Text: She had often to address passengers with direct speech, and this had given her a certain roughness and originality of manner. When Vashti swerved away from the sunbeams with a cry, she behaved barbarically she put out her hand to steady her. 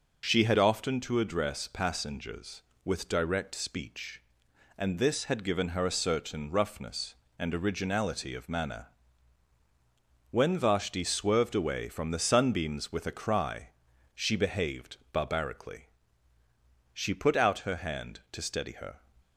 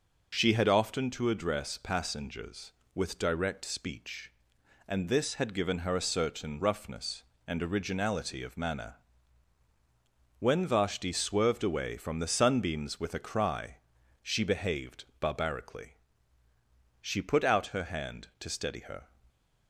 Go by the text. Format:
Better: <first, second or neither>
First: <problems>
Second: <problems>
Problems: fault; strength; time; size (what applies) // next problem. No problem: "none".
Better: neither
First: pauses between "behaved" and "barbarically"; slight; at 14.9 s; 0.16 s long // pauses between "barbarically" and "she"; at 15.8 s; 1.0 s long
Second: pauses between "behaved" and "barbarically"; slight; at 15.0 s; 0.16 s long // pauses between "barbarically" and "she"; at 15.9 s; 1.0 s long